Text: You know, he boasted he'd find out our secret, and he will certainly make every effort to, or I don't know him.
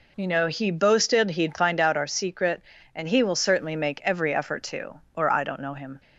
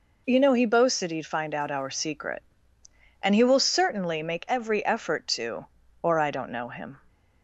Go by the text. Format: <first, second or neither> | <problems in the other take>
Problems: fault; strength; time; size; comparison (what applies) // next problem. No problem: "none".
neither | none